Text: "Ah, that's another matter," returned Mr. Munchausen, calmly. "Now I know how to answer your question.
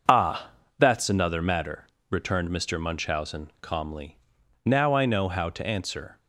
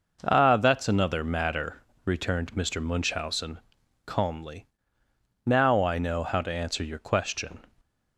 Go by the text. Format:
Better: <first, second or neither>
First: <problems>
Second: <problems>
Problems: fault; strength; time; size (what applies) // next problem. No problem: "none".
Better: second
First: starts louder than the rest; until 1.3 s; 6.5 dB // stops before "your question"; at 6.1 s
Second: none